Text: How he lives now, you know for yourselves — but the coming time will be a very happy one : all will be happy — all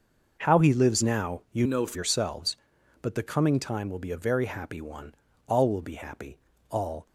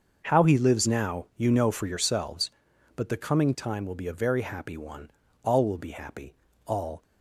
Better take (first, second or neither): second